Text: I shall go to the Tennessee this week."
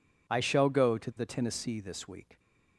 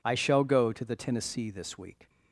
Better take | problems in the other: neither | none

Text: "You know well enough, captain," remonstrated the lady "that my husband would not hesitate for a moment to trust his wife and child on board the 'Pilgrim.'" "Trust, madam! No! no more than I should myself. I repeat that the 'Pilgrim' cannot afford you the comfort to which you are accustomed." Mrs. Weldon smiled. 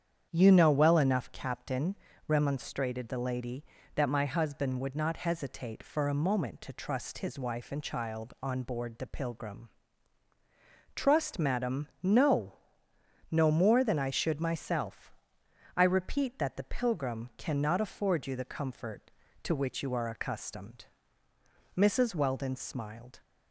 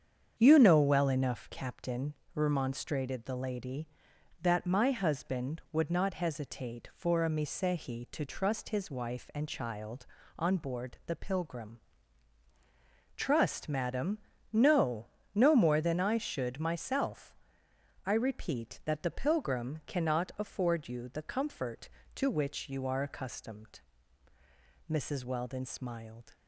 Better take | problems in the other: first | starts louder than the rest; strong; until 1.3 s; 7.5 dB; strong in the first // says "misehi" for "moment"; at 7.2 s

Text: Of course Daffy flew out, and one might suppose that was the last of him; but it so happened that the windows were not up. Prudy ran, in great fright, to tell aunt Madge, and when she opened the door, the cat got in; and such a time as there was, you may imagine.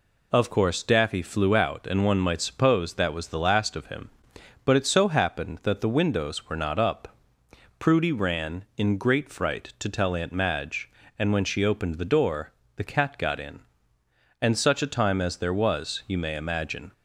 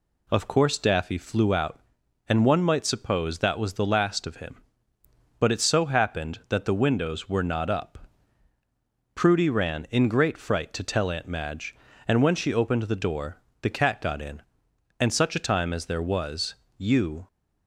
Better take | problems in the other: first | stops before "may imagine"; at 17.2 s

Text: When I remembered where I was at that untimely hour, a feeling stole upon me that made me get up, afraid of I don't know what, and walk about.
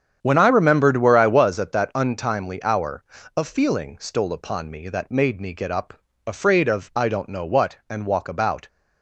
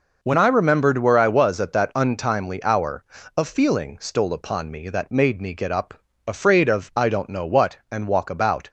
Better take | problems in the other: second | starts louder than the rest; strong; until 1.7 s; 8 dB

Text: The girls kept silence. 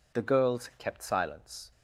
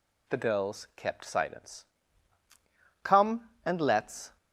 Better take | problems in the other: first | goes on to say "Come and let's"; from 3.0 s on; 1.3 s long

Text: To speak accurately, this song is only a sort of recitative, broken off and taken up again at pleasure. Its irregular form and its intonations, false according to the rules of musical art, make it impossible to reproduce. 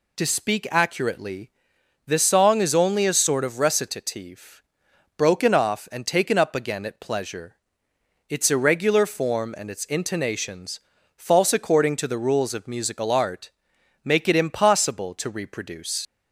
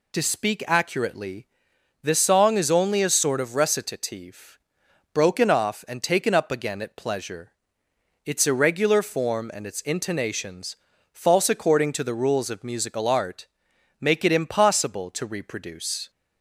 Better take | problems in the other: second | leaves "reproduce" unfinished; at 16.0 s; 85 ms

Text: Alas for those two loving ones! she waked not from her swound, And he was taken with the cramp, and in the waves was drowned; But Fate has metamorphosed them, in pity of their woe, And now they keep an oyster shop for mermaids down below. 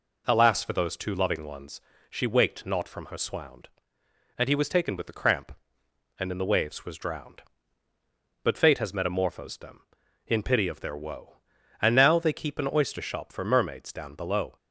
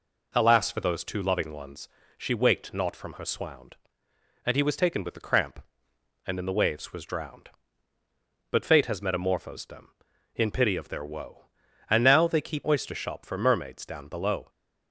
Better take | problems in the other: first | skips "an"; at 12.6 s

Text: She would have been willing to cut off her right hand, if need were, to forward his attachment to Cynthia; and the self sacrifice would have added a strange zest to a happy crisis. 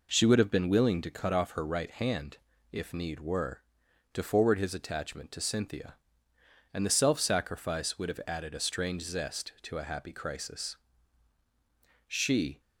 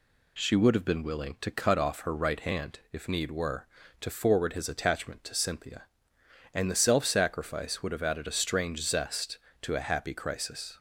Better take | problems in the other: second | goes on to say "She"; from 12.0 s on; 0.52 s long

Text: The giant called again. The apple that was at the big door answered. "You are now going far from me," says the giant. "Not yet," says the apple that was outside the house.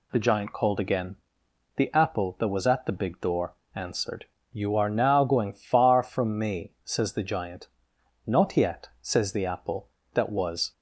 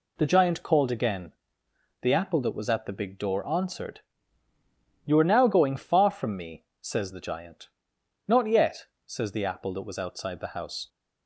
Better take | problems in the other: second | pauses between "door" and "answered"; slight; at 3.5 s; 0.20 s long // stops before "outside the house"; at 10.7 s

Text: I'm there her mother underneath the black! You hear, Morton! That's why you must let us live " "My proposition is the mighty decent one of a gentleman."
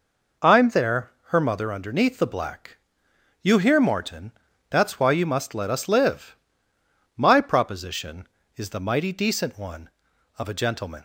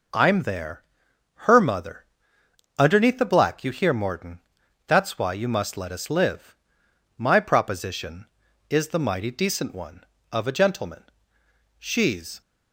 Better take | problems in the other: first | pauses between "there" and "her"; noticeable; at 0.8 s; 0.62 s long; slight in the first // pauses between "mother" and "underneath"; noticeable; at 2.0 s; 0.72 s long // goes on to say "She's"; noticeable; from 11.7 s on; 0.62 s long

